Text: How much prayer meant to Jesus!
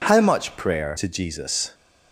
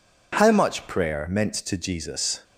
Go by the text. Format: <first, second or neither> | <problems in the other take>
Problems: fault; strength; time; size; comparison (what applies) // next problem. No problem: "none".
second | skips "meant"; at 0.9 s